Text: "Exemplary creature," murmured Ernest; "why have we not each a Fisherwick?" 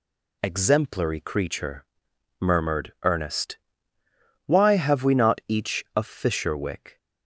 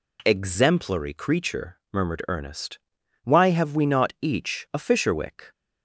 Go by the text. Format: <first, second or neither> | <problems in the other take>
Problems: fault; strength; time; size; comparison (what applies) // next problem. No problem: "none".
neither | none